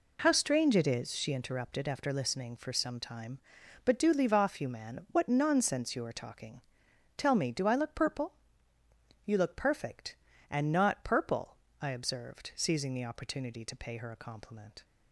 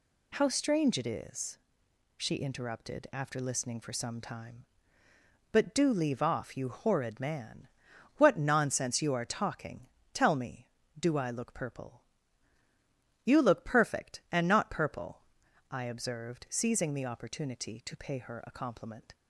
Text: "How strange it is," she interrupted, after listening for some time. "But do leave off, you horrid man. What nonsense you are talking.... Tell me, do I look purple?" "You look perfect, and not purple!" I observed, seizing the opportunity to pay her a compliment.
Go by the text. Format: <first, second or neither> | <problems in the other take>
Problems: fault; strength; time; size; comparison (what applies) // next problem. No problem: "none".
second | skips "horrid"; at 4.6 s